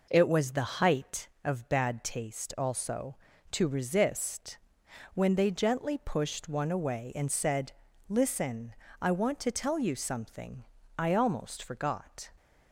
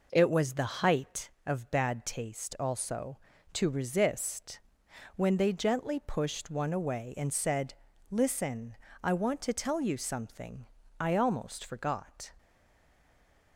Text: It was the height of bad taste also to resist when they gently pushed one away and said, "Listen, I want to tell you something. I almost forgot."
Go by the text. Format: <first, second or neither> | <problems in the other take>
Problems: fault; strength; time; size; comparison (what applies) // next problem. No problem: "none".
first | pauses between "resist" and "when"; noticeable; at 4.5 s; 0.58 s long; noticeable in the first // stays silent after the last word; noticeable; from 12.3 s on; 1.2 s long